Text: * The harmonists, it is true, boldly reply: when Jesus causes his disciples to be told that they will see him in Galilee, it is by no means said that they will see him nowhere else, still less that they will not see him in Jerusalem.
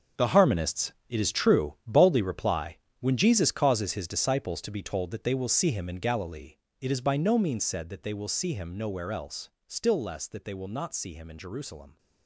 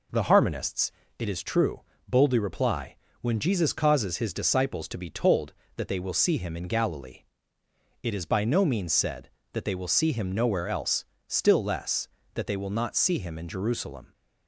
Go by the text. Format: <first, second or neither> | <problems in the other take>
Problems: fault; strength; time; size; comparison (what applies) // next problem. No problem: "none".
second | gets quieter; strong; throughout; 12.5 dB